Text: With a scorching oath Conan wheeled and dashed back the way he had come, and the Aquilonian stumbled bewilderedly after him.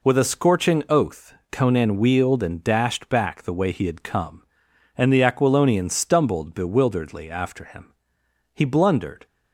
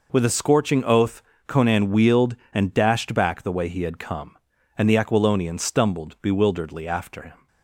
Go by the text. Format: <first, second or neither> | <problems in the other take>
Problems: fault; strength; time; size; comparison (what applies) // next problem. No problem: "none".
second | pauses between "oath" and "Conan"; slight; at 1.3 s; 0.18 s long; slight in the second // goes on to say "He blundered"; noticeable; from 8.5 s on; 0.74 s long